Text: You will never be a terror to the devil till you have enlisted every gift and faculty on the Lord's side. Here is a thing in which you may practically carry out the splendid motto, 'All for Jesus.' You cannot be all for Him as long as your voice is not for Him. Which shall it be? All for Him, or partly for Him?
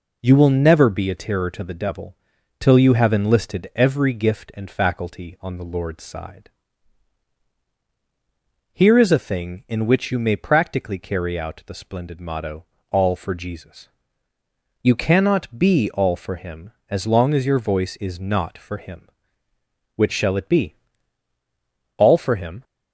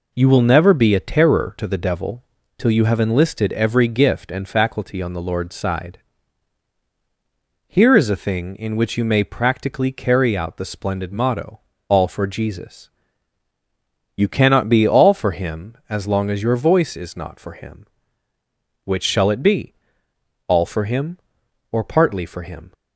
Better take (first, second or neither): second